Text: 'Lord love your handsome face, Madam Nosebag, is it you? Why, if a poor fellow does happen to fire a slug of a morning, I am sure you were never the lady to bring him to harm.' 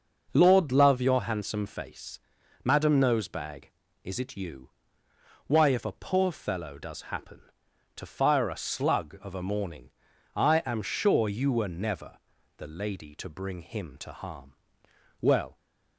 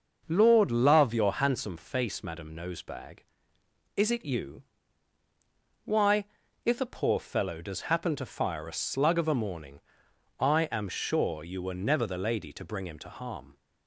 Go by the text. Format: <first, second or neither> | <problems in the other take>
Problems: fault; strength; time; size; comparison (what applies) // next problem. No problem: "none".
second | pauses between "never" and "the"; at 12.1 s; 0.40 s long // goes on to say "Well"; slight; from 15.2 s on; 0.34 s long